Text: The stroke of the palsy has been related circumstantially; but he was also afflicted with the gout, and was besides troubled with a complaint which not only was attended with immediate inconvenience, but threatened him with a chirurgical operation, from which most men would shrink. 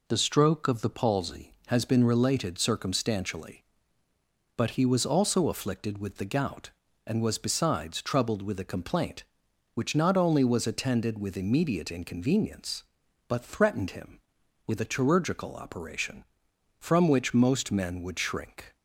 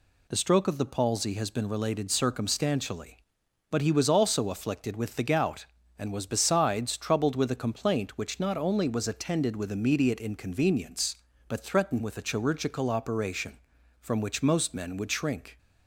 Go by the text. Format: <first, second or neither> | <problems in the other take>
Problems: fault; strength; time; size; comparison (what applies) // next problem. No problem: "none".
first | skips "him"; at 12.0 s